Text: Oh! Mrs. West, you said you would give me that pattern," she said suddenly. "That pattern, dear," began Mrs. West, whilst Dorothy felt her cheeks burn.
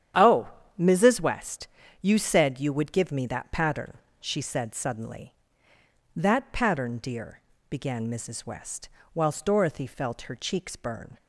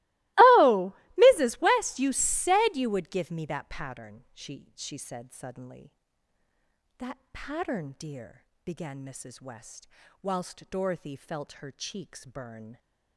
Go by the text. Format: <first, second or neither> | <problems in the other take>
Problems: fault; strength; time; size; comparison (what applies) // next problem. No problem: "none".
first | starts louder than the rest; strong; until 1.5 s; 21.5 dB; strong in the first // says "she" twice; at 4.7 s